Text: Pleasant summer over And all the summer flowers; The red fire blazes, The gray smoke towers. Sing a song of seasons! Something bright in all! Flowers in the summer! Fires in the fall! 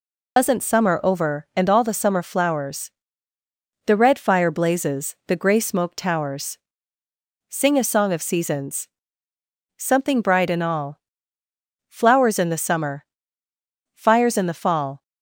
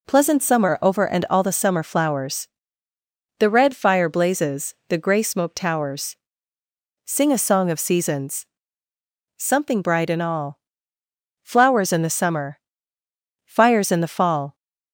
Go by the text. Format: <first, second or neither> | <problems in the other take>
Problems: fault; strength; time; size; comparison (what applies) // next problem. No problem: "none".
second | loses the start of "Pleasant"; at 0.3 s; 125 ms